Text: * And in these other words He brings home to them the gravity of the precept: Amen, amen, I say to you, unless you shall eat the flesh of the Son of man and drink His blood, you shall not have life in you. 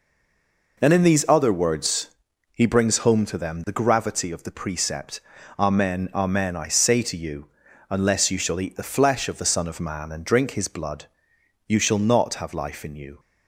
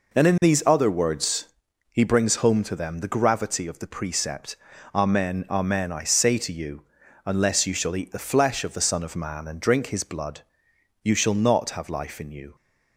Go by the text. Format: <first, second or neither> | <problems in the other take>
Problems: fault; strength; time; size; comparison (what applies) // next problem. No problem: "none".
second | stays silent before the first word; slight; until 0.7 s; 0.7 s long // pauses between "words" and "He"; at 2.1 s; 0.42 s long; also in the second